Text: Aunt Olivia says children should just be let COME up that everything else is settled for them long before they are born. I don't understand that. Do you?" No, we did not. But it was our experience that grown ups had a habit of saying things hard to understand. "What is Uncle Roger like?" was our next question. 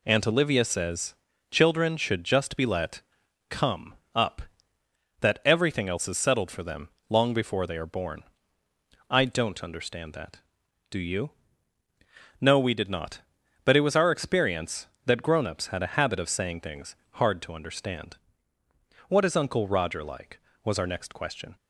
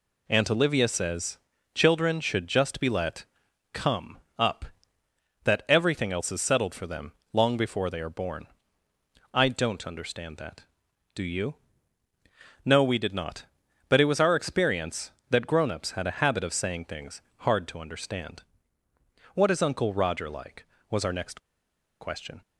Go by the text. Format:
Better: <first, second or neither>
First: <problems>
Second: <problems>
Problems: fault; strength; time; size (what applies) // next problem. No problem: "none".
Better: first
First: pauses between "says" and "children"; at 1.1 s; 0.38 s long // pauses between "let" and "COME"; noticeable; at 3.0 s; 0.48 s long // pauses between "COME" and "up"; slight; at 3.9 s; 0.22 s long // pauses between "them" and "long"; slight; at 6.8 s; 0.20 s long // pauses between "things" and "hard"; slight; at 16.9 s; 0.18 s long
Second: pauses between "says" and "children"; at 1.3 s; 0.38 s long // pauses between "let" and "COME"; noticeable; at 3.2 s; 0.48 s long // pauses between "COME" and "up"; slight; at 4.1 s; 0.22 s long // pauses between "them" and "long"; slight; at 7.1 s; 0.20 s long // pauses between "things" and "hard"; slight; at 17.2 s; 0.18 s long // pauses between "next" and "question"; noticeable; at 21.3 s; 0.61 s long